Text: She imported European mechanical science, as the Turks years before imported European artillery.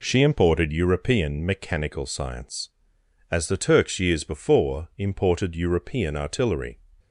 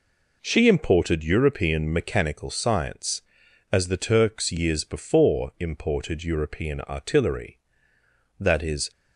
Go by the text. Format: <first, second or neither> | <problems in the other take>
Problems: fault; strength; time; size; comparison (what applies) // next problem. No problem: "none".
first | goes on to say "That is"; from 8.3 s on; 0.52 s long